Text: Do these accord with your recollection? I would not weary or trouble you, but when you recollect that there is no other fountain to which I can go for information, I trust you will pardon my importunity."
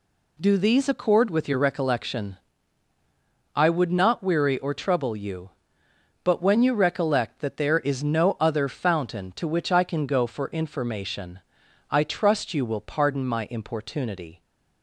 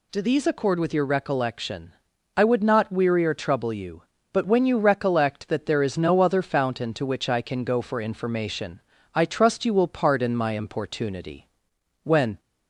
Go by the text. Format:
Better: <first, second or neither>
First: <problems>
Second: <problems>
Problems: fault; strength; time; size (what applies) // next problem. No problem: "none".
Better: first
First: none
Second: goes on to say "When"; slight; from 12.0 s on; 0.38 s long